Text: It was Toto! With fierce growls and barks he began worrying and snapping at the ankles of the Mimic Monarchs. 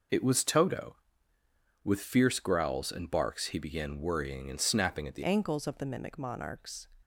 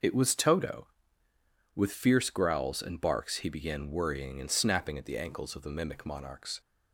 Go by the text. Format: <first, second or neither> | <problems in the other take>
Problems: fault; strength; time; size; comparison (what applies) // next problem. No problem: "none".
second | changes voice at "ankles"; from 5.2 s on; 1.6 s long